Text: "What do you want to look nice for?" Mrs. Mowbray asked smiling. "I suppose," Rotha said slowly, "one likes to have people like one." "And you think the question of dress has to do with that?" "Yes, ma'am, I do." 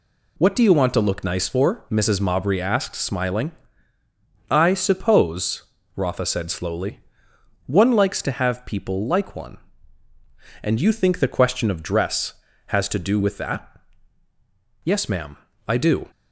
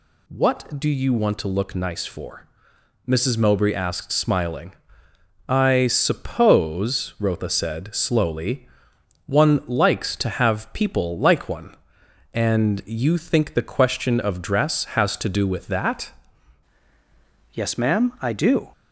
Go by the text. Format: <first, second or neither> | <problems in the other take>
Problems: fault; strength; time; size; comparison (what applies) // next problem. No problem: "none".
first | changes voice at "Yes"; from 17.5 s on; 1.2 s long